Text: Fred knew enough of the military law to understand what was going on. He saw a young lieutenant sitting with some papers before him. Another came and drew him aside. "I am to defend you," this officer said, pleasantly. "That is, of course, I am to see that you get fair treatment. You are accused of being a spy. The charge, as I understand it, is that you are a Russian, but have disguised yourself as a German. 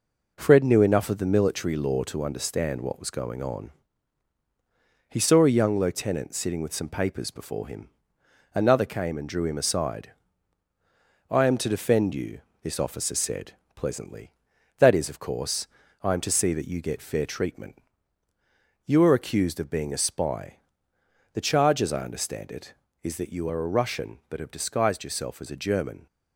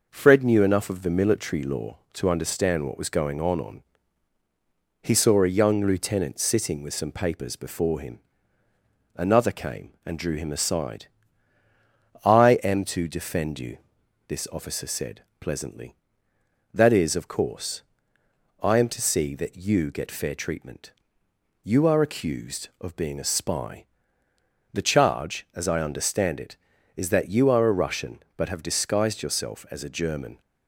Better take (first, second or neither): first